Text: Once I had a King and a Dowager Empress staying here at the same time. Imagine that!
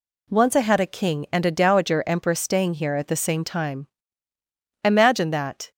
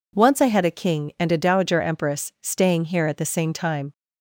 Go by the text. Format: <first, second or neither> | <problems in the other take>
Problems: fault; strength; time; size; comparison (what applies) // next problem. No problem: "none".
first | stops before "Imagine that"; at 3.9 s